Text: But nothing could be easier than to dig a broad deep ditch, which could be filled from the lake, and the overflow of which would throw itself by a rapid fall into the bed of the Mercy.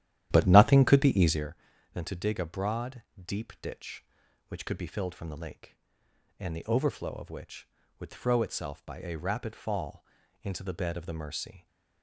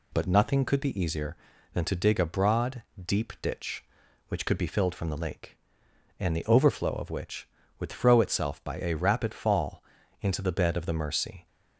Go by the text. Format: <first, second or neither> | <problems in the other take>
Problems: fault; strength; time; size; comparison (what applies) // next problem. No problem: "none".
second | starts louder than the rest; strong; until 1.5 s; 12 dB // pauses between "broad" and "deep"; slight; at 3.0 s; 0.22 s long; slight in the second // pauses between "fall" and "into"; at 10.0 s; 0.38 s long; also in the second